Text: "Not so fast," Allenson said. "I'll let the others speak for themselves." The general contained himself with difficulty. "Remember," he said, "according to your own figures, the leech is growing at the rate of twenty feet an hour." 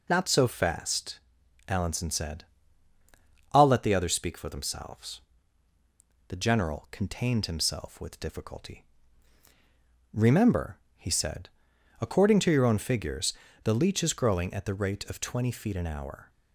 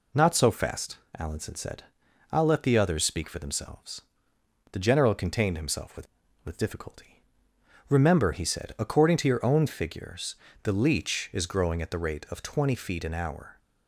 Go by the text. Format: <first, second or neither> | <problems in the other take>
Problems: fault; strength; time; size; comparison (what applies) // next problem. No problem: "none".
first | says "with" twice; at 6.4 s